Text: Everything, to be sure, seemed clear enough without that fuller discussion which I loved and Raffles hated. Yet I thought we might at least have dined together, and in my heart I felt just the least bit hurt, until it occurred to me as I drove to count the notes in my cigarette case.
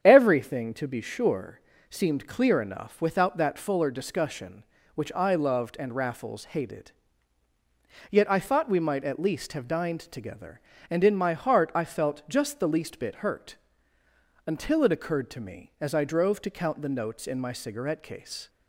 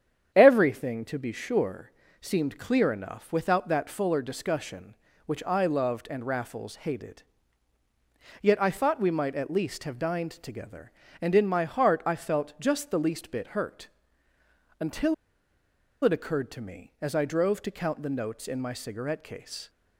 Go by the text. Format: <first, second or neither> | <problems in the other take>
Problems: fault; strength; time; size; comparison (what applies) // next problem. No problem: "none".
first | starts louder than the rest; strong; until 1.3 s; 8.5 dB; strong in the first // pauses between "until" and "it"; noticeable; at 15.1 s; 0.88 s long